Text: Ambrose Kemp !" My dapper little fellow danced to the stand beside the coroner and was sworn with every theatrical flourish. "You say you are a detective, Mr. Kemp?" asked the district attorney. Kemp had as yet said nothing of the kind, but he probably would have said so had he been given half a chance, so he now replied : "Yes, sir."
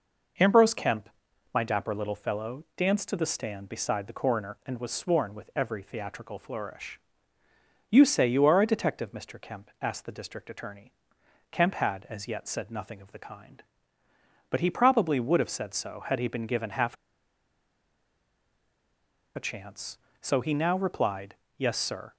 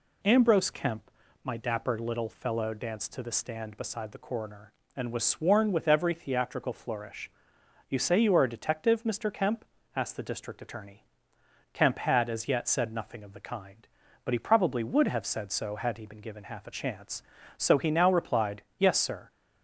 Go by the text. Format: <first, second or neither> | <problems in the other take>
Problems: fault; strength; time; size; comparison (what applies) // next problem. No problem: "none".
second | pauses between "half" and "a"; strong; at 16.9 s; 2.4 s long